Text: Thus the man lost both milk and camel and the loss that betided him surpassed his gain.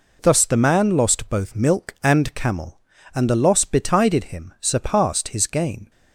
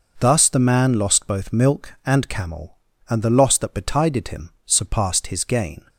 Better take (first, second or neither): second